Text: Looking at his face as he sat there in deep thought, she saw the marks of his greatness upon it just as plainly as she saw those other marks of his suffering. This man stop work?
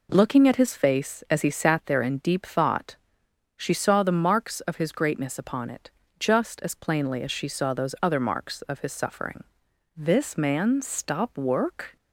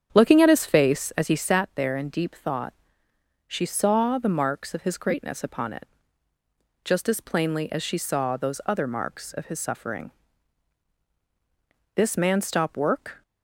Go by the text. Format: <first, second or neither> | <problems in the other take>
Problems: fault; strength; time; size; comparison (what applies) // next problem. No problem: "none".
first | starts louder than the rest; strong; until 1.5 s; 8.5 dB // pauses between "it" and "just"; noticeable; at 5.8 s; 0.96 s long; slight in the first